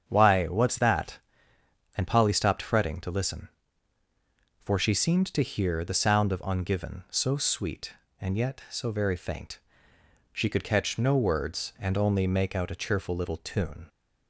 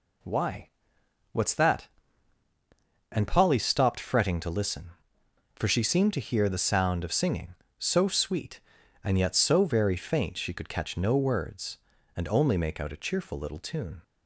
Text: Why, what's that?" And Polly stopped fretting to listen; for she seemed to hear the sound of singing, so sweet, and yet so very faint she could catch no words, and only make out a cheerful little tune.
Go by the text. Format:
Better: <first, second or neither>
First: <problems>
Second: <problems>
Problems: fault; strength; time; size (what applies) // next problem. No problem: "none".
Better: second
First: starts louder than the rest; strong; until 1.0 s; 8 dB // says "ungiven" for "singing"; at 6.4 s // pauses between "faint" and "she"; noticeable; at 9.5 s; 0.74 s long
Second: none